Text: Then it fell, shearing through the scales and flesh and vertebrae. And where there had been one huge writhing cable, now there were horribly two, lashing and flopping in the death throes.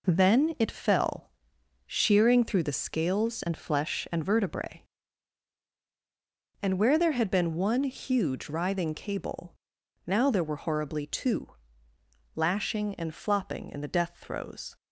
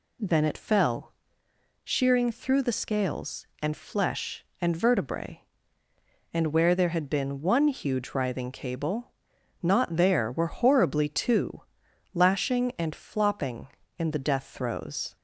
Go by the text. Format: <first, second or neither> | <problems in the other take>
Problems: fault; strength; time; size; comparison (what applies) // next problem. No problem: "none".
first | says "not" for "now"; at 9.6 s